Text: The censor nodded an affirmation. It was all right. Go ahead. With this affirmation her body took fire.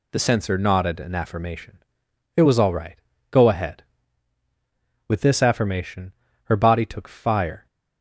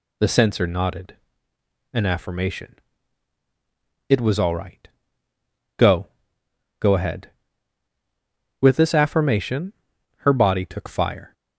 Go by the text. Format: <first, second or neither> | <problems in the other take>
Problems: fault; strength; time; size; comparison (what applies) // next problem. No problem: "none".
first | pauses between "nodded" and "an"; noticeable; at 1.1 s; 0.76 s long // says "Go" twice; at 6.7 s // pauses between "affirmation" and "her"; at 9.7 s; 0.45 s long; slight in the first